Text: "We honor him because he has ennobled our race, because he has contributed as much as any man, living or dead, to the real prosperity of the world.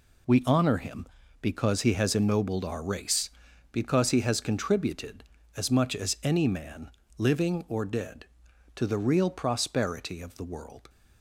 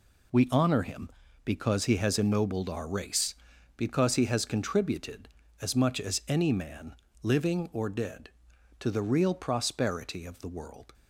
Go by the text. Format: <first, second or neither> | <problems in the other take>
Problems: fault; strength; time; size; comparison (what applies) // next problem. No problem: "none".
neither | none